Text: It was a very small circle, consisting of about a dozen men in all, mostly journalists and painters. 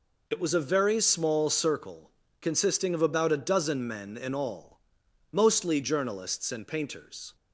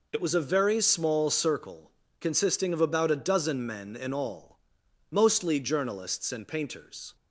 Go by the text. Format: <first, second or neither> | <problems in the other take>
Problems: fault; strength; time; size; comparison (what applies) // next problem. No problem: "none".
neither | none